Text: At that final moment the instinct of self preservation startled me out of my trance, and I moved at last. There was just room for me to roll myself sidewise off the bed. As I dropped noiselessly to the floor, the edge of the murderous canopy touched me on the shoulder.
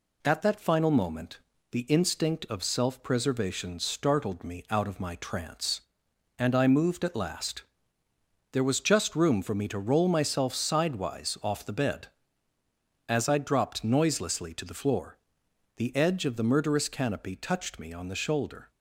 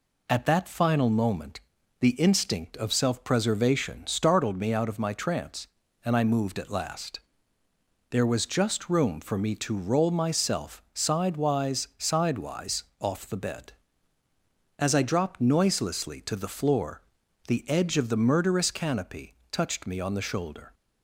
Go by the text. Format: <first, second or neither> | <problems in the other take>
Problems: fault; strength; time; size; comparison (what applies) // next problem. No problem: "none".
first | pauses between "moment" and "the"; at 1.5 s; 0.40 s long; slight in the first // says "sidewise" twice; at 11.9 s // pauses between "canopy" and "touched"; slight; at 19.3 s; 0.18 s long